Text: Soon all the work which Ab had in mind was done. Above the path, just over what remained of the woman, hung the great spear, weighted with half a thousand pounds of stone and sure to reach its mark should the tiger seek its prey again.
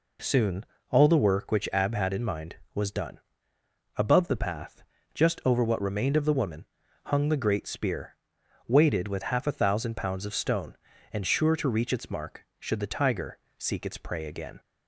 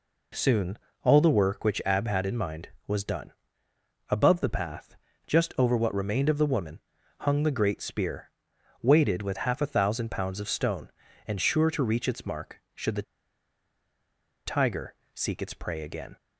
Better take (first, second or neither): first